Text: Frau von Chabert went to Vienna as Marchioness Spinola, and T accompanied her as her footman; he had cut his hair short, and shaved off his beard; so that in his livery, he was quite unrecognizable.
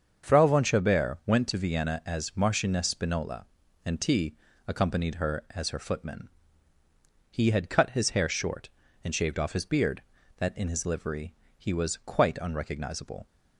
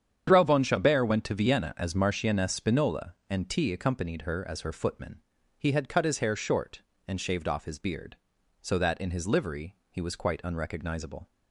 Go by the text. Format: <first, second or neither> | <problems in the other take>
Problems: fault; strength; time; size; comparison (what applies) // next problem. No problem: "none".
second | starts louder than the rest; until 1.3 s; 7 dB; strong in the second // pauses between "T" and "accompanied"; slight; at 4.3 s; 0.28 s long // skips "so"; at 10.1 s